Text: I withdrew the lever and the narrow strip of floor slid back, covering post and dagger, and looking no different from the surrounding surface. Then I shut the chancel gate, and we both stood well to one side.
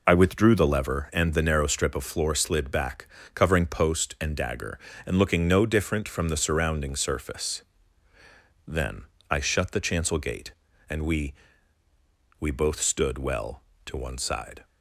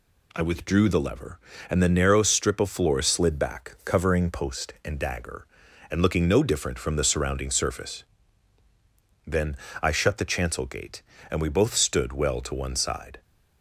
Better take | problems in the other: second | pauses between "Then" and "I"; slight; at 9.0 s; 0.26 s long; slight in the second // says "we" twice; at 12.3 s

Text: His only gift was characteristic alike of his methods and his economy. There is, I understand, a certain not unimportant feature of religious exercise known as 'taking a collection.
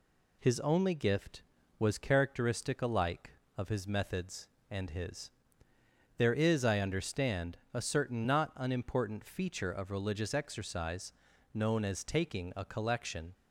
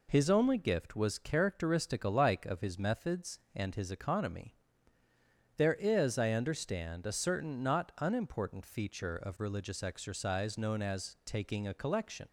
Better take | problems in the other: second | skips "economy"; at 5.7 s // pauses between "exercise" and "known"; at 11.1 s; 0.44 s long

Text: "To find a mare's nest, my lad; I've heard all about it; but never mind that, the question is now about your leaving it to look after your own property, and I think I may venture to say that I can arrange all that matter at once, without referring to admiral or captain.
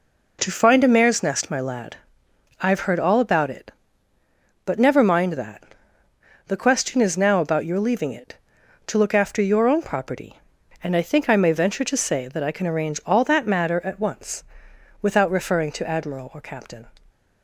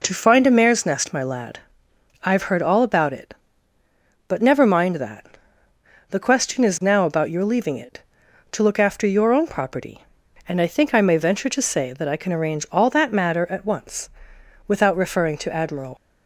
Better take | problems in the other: first | stops before "or captain"; at 15.9 s

